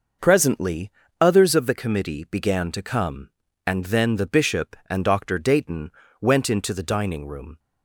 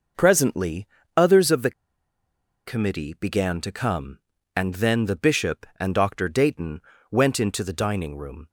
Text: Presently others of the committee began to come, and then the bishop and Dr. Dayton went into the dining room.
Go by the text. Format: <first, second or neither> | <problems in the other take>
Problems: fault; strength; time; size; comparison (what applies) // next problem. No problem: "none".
first | pauses between "Presently" and "others"; slight; at 0.8 s; 0.30 s long; slight in the first // pauses between "the" and "committee"; noticeable; at 1.7 s; 0.95 s long // pauses between "Dayton" and "went"; slight; at 6.8 s; 0.30 s long; slight in the first